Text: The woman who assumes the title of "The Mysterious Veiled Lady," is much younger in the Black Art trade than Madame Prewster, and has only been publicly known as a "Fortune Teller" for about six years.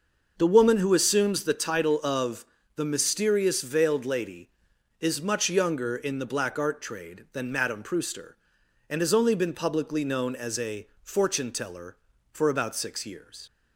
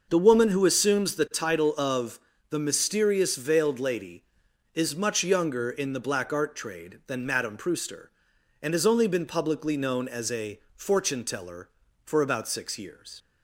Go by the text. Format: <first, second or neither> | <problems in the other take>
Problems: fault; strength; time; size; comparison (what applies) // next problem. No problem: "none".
neither | pauses between "of" and "The"; slight; the same in both // pauses between "a" and "Fortune"; slight; the same in both